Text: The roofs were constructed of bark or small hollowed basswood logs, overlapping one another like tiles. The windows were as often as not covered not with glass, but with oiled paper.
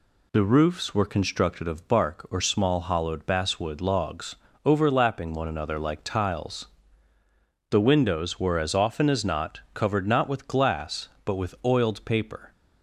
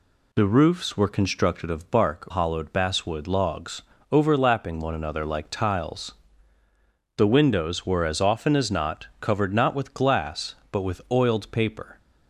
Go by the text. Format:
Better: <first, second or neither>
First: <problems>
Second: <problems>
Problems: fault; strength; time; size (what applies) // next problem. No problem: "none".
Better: first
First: none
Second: skips "or small"; at 2.2 s